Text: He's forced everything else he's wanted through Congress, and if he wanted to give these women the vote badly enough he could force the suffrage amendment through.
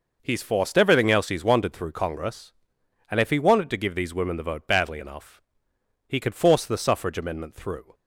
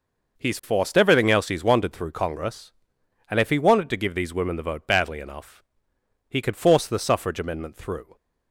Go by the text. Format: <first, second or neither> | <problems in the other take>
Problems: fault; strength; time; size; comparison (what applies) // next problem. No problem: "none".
neither | pauses between "enough" and "he"; noticeable; the same in both